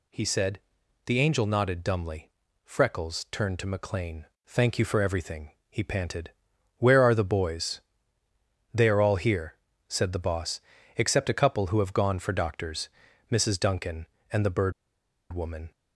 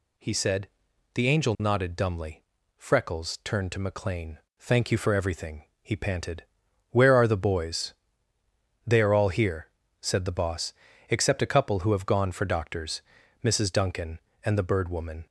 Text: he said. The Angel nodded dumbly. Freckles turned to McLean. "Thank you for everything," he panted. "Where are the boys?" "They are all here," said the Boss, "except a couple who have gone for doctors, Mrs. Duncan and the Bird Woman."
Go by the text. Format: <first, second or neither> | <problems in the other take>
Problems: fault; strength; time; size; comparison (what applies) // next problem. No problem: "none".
second | pauses between "Bird" and "Woman"; noticeable; at 14.7 s; 0.60 s long